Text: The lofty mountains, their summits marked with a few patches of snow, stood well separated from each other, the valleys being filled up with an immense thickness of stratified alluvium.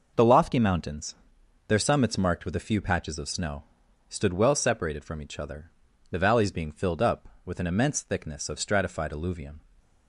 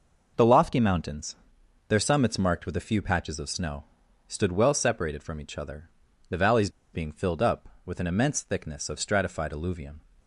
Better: first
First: none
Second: pauses between "valleys" and "being"; slight; at 6.7 s; 0.22 s long

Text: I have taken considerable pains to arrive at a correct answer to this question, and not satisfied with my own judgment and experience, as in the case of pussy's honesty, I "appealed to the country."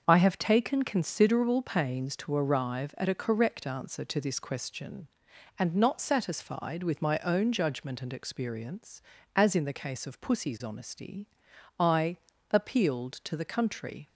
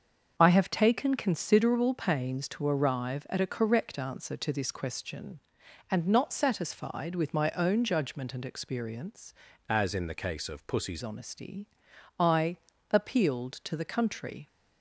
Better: first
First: starts louder than the rest; until 1.0 s; 6.5 dB // pauses between "I" and "appealed"; at 12.1 s; 0.38 s long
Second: starts louder than the rest; until 1.3 s; 6.5 dB // changes voice from "as" to "pussy's"; from 9.6 to 11.0 s; 1.4 s long // pauses between "I" and "appealed"; at 12.5 s; 0.38 s long

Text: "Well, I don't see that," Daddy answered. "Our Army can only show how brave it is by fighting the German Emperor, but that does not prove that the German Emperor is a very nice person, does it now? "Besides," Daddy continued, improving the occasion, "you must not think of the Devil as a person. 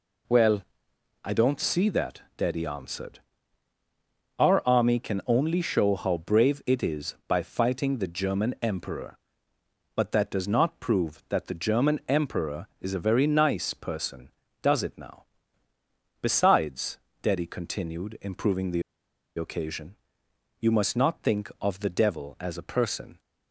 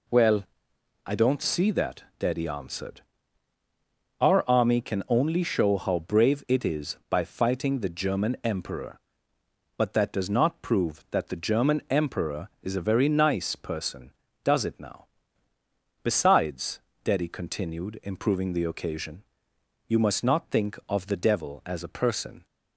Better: second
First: pauses between "the" and "occasion"; noticeable; at 18.8 s; 0.55 s long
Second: none

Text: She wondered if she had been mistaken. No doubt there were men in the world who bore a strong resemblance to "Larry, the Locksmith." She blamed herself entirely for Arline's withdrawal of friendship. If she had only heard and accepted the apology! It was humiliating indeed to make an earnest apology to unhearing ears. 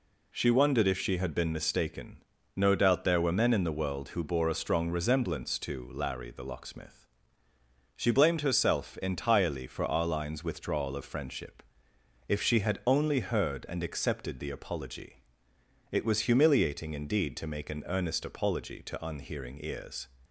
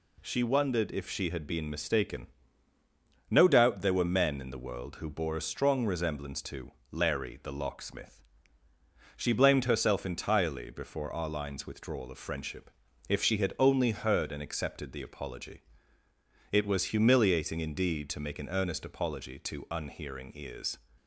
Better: first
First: none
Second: pauses between "to" and "Larry"; slight; at 6.7 s; 0.20 s long // says "before" for "for"; at 10.7 s

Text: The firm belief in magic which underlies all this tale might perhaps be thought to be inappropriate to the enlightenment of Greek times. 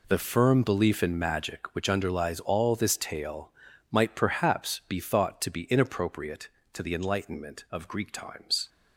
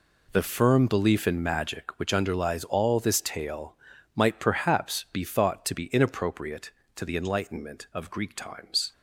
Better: neither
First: pauses between "tale" and "might"; at 3.4 s; 0.40 s long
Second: pauses between "tale" and "might"; at 3.7 s; 0.40 s long

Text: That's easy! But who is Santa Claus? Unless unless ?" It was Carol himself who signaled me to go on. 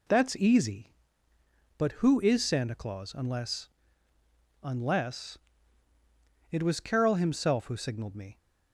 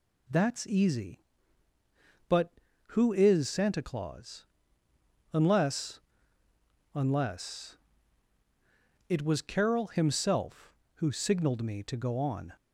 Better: second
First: pauses between "Unless" and "unless"; noticeable; at 3.6 s; 0.96 s long // stops before "to go on"; at 8.3 s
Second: pauses between "Unless" and "unless"; noticeable; at 6.0 s; 0.96 s long

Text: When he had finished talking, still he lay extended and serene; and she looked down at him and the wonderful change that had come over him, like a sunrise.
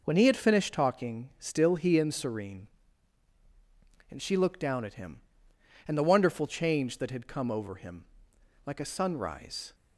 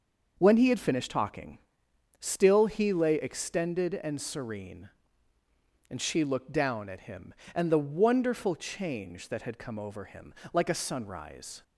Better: second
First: skips "lay extended"; at 1.9 s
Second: none

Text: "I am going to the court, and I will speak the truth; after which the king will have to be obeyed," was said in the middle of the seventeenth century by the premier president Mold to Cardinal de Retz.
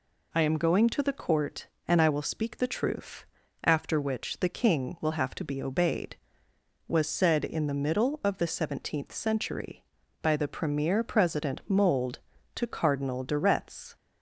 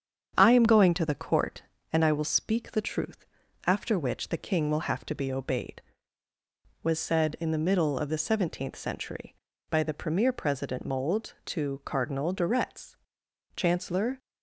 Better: first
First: none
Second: starts louder than the rest; strong; until 1.3 s; 8 dB // goes on to say "Chancellor"; noticeable; from 13.5 s on; 0.64 s long

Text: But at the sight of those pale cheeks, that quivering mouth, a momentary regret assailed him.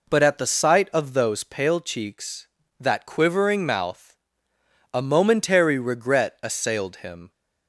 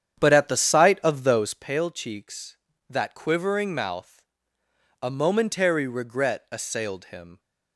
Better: first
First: none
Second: starts louder than the rest; strong; until 1.7 s; 9 dB

